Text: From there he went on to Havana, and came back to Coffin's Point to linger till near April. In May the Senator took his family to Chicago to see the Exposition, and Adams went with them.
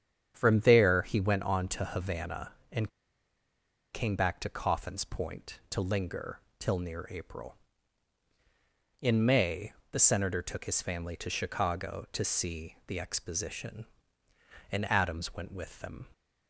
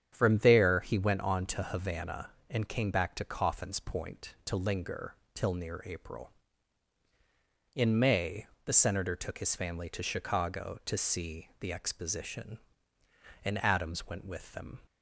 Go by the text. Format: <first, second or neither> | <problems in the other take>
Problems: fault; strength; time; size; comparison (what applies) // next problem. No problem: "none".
second | starts louder than the rest; strong; until 1.3 s; 8.5 dB; strong in the second // pauses between "and" and "came"; at 2.8 s; 1.0 s long // pauses between "linger" and "till"; slight; at 6.4 s; 0.18 s long; slight in the second // pauses between "May" and "the"; slight; at 9.7 s; 0.20 s long; slight in the second